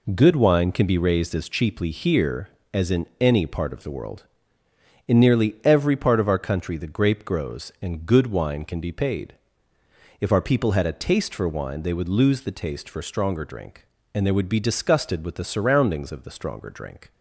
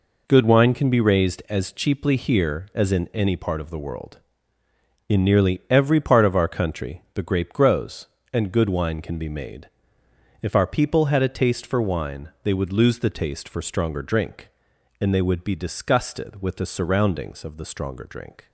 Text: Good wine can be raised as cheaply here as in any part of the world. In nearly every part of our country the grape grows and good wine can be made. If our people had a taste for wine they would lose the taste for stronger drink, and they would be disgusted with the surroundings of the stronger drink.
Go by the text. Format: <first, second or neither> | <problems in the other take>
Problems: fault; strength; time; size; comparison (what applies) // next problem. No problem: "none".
second | says "paid" for "made"; at 8.9 s